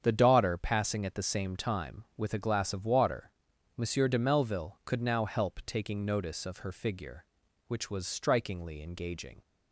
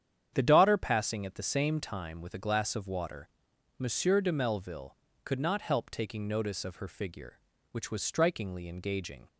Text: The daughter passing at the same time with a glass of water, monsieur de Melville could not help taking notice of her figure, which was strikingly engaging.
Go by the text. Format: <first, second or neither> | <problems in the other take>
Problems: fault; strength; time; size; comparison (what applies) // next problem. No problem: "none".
second | starts louder than the rest; strong; until 1.0 s; 8 dB; strong in the second // says "now" for "not"; at 5.0 s